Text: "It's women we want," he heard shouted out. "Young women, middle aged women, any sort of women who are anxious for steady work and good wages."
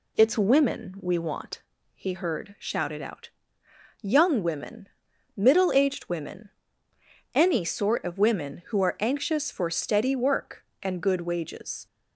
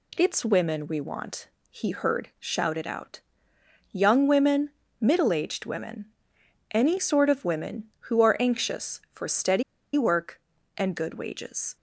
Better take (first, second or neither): first